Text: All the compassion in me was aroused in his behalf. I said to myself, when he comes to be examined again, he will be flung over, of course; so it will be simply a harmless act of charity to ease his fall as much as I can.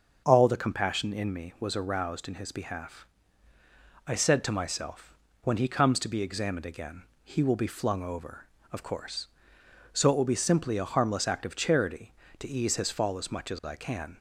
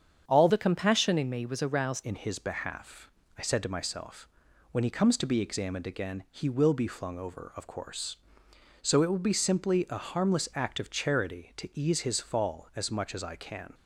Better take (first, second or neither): first